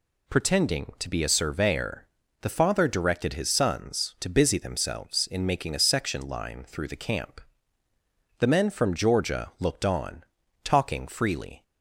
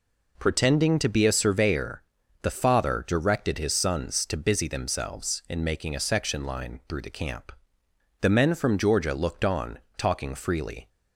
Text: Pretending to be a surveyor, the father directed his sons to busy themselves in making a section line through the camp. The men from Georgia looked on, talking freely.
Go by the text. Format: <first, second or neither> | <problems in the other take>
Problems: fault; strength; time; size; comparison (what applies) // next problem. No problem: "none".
neither | none